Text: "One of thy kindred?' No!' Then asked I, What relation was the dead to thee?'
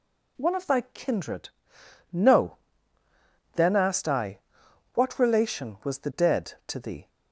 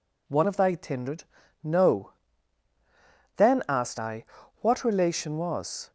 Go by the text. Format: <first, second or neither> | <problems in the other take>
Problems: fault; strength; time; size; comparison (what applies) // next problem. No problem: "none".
first | stops before "the dead to thee"; at 5.8 s